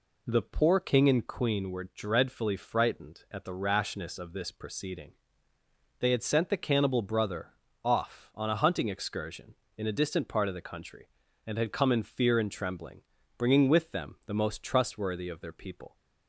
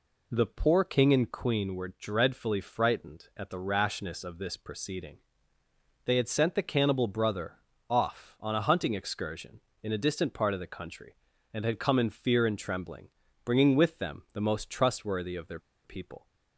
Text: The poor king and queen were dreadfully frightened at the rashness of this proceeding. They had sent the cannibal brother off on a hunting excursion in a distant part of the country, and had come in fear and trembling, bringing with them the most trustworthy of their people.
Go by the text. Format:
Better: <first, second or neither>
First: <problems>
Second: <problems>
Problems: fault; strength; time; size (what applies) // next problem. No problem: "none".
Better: first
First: pauses between "brother" and "off"; slight; at 7.4 s; 0.34 s long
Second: pauses between "brother" and "off"; slight; at 7.5 s; 0.34 s long // pauses between "their" and "people"; slight; at 15.5 s; 0.25 s long